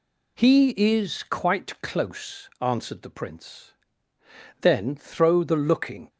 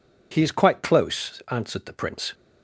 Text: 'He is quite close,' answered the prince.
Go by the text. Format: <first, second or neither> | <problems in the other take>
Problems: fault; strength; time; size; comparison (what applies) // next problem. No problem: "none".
second | goes on to say "Then throw the looking"; from 4.6 s on; 1.4 s long